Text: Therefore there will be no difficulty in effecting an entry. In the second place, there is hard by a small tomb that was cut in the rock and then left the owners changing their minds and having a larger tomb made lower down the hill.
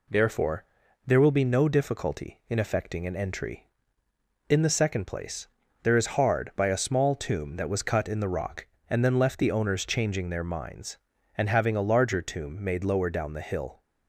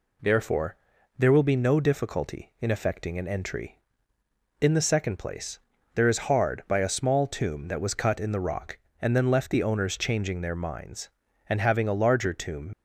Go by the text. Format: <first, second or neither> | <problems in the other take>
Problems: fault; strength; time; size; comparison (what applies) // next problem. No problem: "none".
first | pauses between "Therefore" and "there"; at 0.7 s; 0.42 s long; also in the first // stops before "made lower down the hill"; at 12.7 s